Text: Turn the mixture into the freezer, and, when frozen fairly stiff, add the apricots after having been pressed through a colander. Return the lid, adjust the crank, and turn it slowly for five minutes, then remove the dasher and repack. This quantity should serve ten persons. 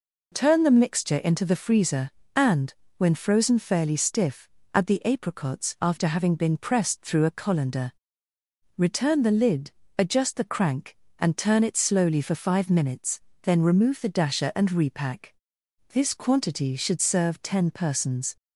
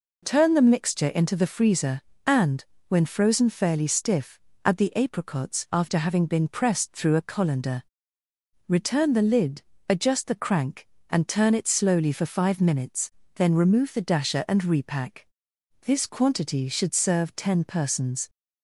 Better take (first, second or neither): neither